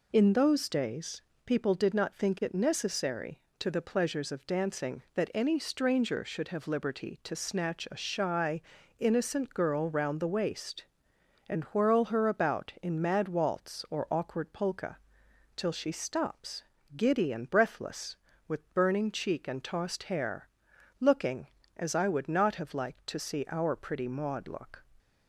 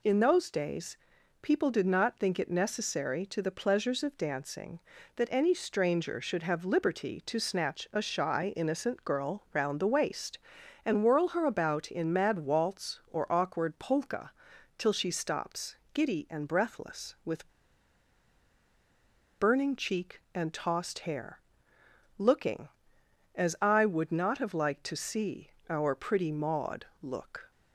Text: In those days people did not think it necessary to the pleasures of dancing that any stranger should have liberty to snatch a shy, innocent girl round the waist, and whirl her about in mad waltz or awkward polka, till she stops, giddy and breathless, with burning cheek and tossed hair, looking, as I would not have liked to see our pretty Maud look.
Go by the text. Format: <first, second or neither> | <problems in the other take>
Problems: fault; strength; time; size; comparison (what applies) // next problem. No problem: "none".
first | pauses between "days" and "people"; at 0.9 s; 0.44 s long; slight in the first // pauses between "with" and "burning"; strong; at 17.4 s; 1.9 s long // pauses between "see" and "our"; slight; at 25.4 s; 0.22 s long // pauses between "Maud" and "look"; slight; at 26.8 s; 0.16 s long